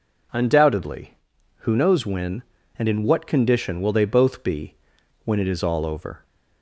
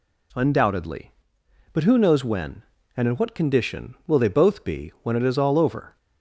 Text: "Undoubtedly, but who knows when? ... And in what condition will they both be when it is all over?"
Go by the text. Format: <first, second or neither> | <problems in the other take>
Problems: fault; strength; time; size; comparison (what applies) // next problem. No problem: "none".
second | skips "but"; at 1.3 s // pauses between "be" and "when"; noticeable; at 4.7 s; 0.50 s long